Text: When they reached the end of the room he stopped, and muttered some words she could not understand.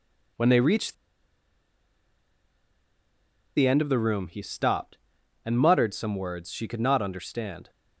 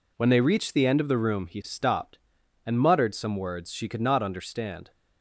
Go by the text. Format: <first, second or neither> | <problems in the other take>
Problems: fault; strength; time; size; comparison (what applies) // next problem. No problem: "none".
second | pauses between "reached" and "the"; strong; at 0.9 s; 2.6 s long